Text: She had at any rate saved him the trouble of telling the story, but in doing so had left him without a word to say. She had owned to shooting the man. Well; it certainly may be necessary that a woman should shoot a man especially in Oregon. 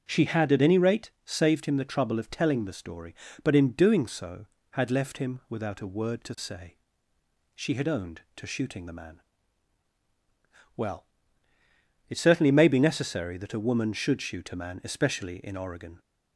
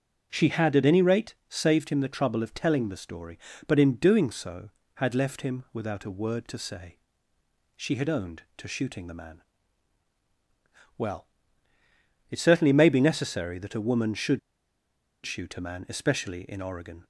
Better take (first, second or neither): first